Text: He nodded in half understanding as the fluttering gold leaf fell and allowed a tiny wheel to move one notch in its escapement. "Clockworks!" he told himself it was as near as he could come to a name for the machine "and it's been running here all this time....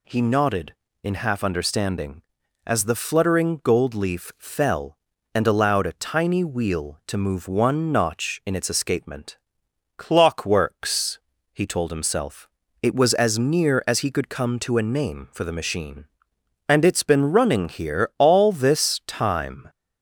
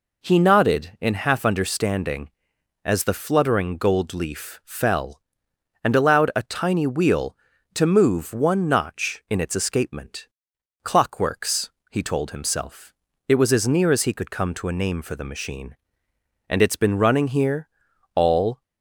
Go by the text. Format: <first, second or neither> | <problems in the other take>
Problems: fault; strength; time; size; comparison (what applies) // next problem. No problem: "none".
first | pauses between "himself" and "it"; slight; at 12.9 s; 0.32 s long; slight in the first // pauses between "here" and "all"; noticeable; at 17.6 s; 0.48 s long // stops before "this time"; at 18.6 s